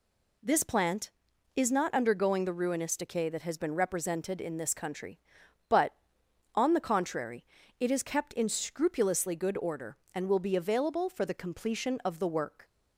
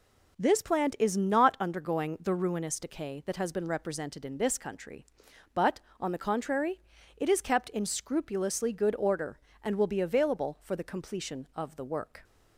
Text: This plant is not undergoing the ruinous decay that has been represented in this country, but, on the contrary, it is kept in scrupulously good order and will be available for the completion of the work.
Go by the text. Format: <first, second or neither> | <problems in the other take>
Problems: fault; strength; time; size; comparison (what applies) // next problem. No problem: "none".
neither | none